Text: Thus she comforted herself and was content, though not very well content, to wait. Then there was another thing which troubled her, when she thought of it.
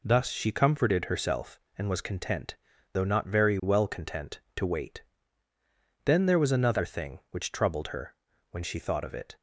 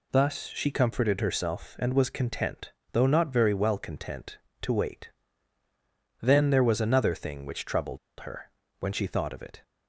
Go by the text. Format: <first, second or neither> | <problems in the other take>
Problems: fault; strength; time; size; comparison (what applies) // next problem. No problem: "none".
first | pauses between "troubled" and "her"; slight; at 7.9 s; 0.22 s long